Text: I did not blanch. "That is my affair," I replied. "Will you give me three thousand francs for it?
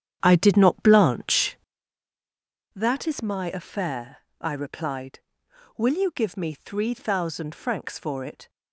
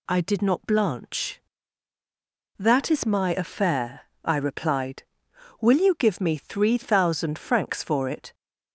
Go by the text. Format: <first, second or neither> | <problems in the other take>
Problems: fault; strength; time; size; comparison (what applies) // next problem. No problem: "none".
second | starts louder than the rest; strong; until 2.0 s; 9.5 dB